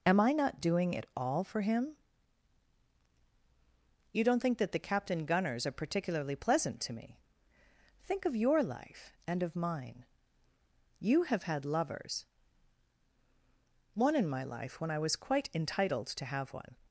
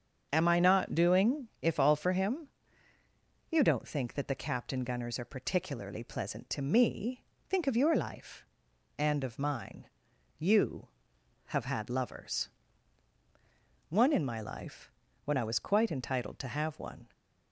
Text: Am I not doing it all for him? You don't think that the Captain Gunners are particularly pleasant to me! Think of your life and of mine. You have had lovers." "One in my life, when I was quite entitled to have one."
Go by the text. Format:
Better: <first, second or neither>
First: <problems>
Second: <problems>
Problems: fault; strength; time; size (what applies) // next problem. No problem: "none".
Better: first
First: none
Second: starts louder than the rest; until 1.3 s; 7 dB // says "if" for "it"; at 1.6 s